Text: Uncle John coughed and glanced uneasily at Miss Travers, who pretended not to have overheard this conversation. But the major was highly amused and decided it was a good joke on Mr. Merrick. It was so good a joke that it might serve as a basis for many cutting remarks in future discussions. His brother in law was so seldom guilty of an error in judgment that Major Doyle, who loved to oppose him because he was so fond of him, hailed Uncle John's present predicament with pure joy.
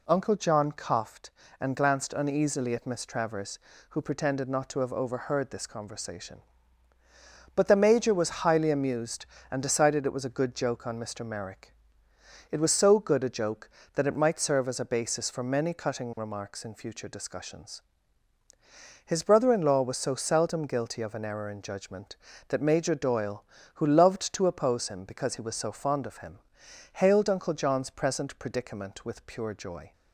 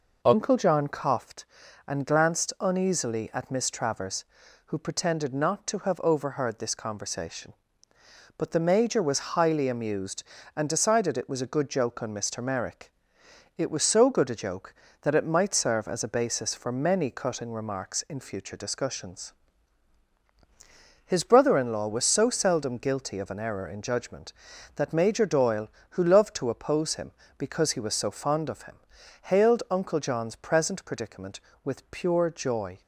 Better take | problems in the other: neither | none

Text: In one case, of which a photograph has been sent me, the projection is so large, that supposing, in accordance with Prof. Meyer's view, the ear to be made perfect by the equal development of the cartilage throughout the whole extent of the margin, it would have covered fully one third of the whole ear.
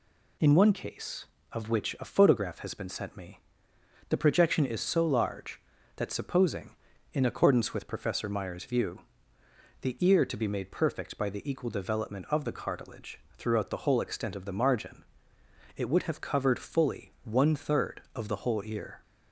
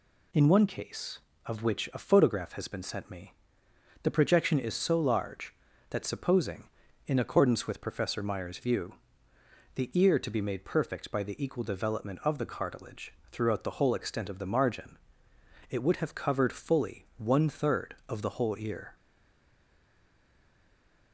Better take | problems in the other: first | pauses between "cartilage" and "throughout"; slight; at 13.1 s; 0.16 s long; slight in the first // stays silent after the last word; from 18.9 s on; 2.2 s long

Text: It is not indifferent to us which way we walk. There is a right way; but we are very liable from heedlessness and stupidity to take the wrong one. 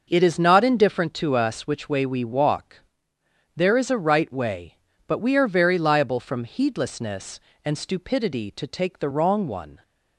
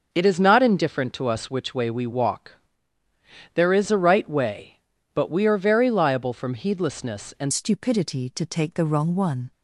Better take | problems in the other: first | starts louder than the rest; until 1.1 s; 6.5 dB // changes voice at "stupidity"; from 7.5 s on; 2.0 s long

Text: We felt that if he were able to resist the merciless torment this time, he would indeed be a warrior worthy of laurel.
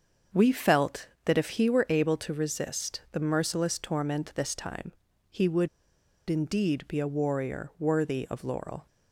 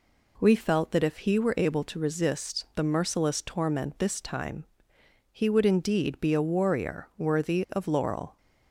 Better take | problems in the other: second | starts louder than the rest; until 1.5 s; 6.5 dB // pauses between "would" and "indeed"; noticeable; at 5.6 s; 0.59 s long

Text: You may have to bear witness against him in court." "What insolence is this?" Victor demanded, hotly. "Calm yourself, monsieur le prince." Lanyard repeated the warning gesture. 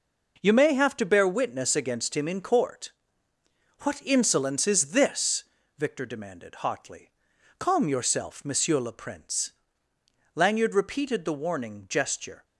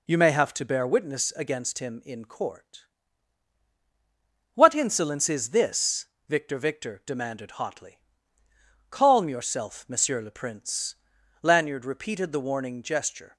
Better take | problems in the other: first | says "Victor" twice; at 6.5 s

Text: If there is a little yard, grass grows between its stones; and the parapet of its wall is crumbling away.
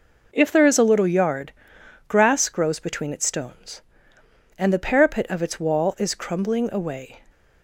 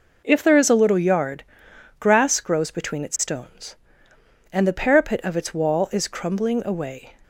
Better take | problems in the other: neither | none

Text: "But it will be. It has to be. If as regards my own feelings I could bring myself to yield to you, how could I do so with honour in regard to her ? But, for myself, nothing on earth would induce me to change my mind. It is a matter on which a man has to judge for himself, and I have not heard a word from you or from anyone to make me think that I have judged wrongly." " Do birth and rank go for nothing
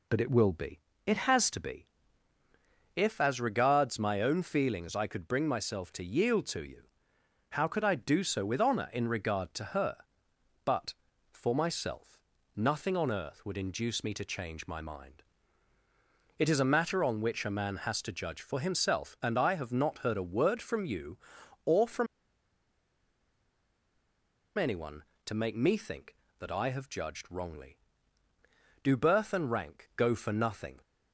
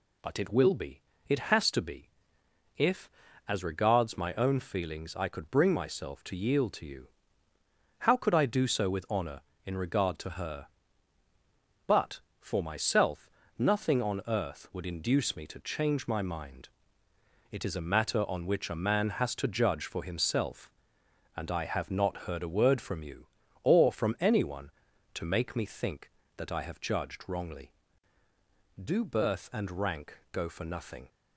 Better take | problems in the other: second | pauses between "from" and "anyone"; strong; at 22.0 s; 2.5 s long

